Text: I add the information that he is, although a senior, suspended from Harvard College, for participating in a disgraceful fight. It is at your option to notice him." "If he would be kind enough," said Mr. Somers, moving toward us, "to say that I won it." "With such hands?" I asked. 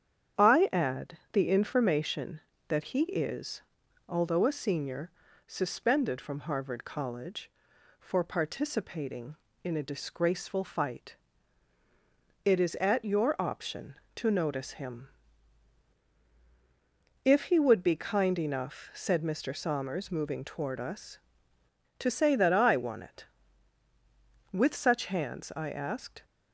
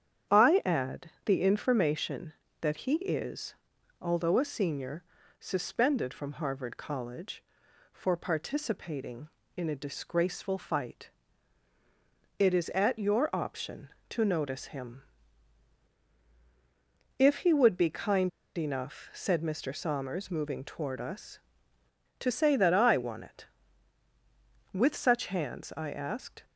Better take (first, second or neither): first